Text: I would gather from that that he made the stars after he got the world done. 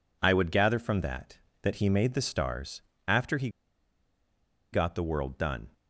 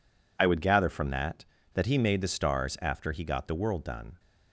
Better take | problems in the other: second | pauses between "stars" and "after"; slight; at 2.8 s; 0.26 s long // pauses between "he" and "got"; at 3.4 s; 1.2 s long

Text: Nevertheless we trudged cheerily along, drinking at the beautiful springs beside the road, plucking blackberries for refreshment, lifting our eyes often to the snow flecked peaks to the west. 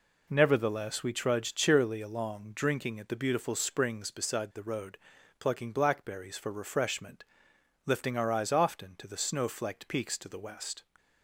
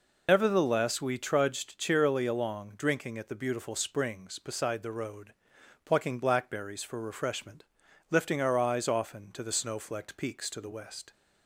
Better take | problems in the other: first | loses the start of "Nevertheless"; at 0.2 s; 100 ms

